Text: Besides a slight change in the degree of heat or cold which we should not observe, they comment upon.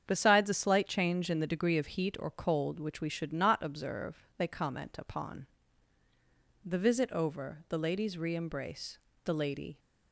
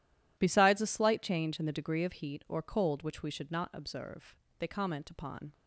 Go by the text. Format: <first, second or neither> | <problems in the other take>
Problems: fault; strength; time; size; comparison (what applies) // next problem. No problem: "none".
second | starts louder than the rest; strong; until 1.0 s; 8 dB // goes on to say "The visit over the ladies re embrace the lady"; strong; from 6.6 s on; 3.1 s long